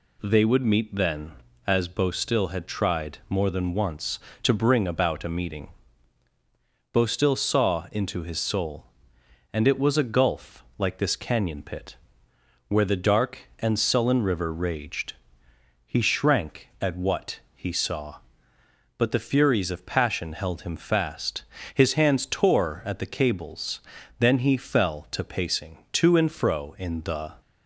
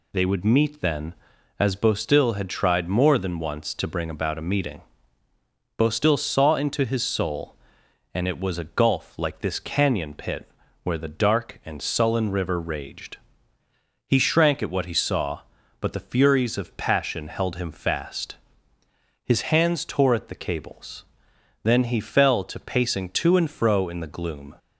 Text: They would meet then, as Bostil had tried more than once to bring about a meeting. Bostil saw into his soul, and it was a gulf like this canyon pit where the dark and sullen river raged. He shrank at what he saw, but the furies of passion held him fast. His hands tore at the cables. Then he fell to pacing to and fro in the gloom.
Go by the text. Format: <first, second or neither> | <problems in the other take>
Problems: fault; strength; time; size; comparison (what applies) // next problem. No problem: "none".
second | pauses between "pit" and "where"; noticeable; at 11.9 s; 0.72 s long; slight in the second // pauses between "what" and "he"; slight; at 17.4 s; 0.16 s long // stops before "gloom"; at 27.4 s